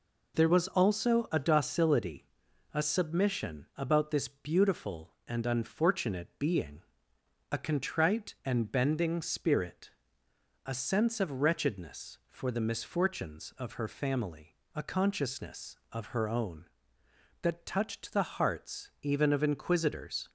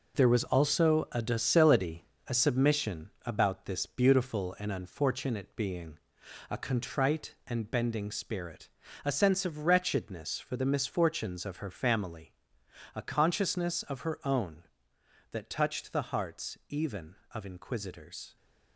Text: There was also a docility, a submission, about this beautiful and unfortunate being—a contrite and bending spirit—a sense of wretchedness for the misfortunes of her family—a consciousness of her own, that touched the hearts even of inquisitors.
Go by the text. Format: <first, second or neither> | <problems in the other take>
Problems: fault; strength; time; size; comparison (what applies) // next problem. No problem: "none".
first | gets quieter; strong; throughout; 8 dB